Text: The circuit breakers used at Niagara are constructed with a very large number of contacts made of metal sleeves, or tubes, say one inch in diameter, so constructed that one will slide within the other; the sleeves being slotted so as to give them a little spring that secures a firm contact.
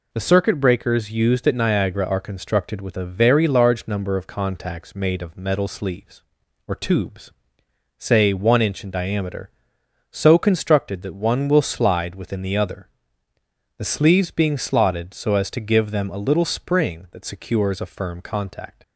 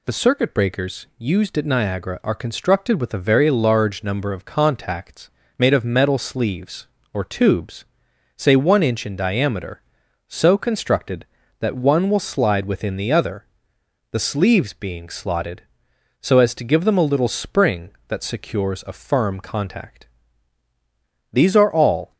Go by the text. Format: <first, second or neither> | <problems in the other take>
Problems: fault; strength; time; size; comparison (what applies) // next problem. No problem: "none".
first | pauses between "contacts" and "made"; slight; at 5.2 s; 0.28 s long // goes on to say "These are all"; noticeable; from 21.3 s on; 0.82 s long